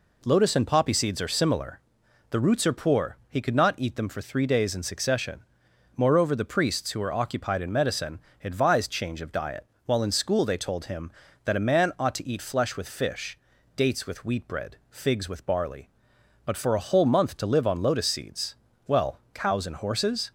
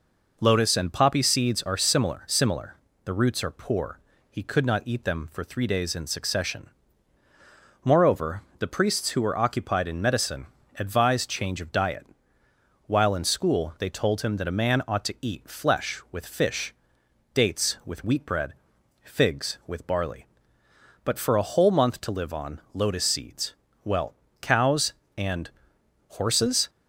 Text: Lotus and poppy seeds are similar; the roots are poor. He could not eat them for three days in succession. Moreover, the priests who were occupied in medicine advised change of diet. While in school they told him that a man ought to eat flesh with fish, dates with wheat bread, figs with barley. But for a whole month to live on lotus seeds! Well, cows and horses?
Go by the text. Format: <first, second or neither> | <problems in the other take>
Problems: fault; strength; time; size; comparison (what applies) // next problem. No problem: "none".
first | says "similar" twice; at 2.2 s // pauses between "medicine" and "advised"; slight; at 10.4 s; 0.32 s long; slight in the first // pauses between "and" and "horses"; noticeable; at 25.4 s; 0.60 s long